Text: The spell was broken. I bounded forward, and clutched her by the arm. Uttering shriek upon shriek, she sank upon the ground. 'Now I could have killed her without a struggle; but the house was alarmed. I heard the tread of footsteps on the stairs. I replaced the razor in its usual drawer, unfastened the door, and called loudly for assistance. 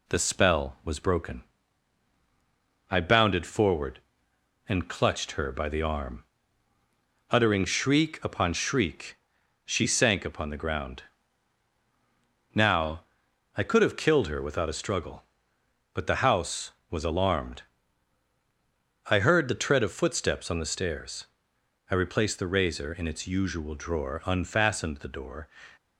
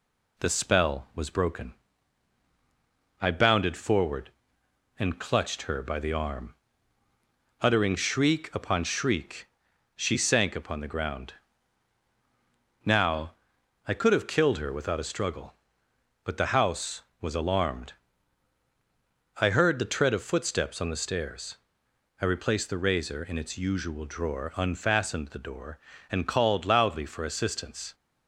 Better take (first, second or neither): second